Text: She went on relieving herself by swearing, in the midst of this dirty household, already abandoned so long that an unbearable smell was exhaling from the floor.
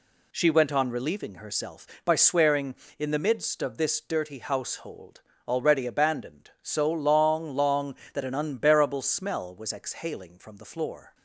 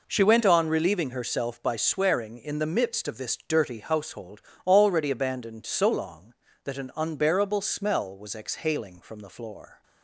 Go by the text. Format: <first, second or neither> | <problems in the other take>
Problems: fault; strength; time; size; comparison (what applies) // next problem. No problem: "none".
second | says "long" twice; at 7.5 s